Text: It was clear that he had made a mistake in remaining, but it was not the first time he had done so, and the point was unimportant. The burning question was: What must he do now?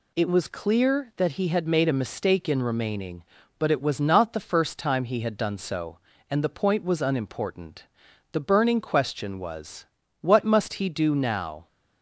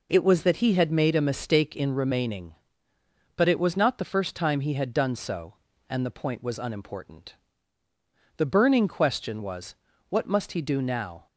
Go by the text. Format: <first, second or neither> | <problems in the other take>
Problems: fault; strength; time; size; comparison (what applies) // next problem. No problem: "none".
first | skips "clear"; at 0.4 s